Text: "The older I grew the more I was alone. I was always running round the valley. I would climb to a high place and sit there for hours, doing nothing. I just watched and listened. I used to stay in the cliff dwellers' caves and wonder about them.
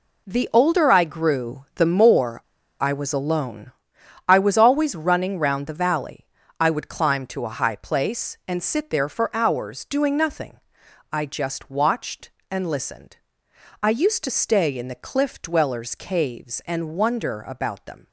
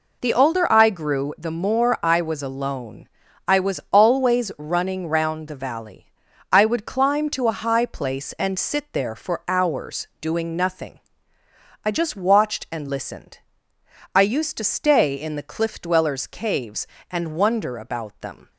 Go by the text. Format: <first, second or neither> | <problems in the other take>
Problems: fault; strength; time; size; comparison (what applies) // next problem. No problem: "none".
second | pauses between "more" and "I"; at 2.4 s; 0.39 s long